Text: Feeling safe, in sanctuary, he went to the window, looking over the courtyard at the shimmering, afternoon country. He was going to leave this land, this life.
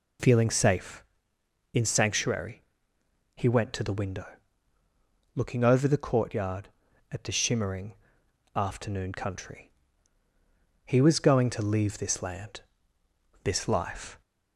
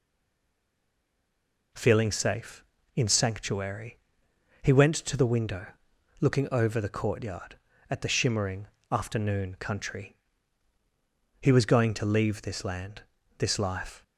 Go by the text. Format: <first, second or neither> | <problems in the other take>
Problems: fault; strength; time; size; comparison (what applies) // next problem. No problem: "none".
first | stays silent before the first word; noticeable; until 1.7 s; 1.7 s long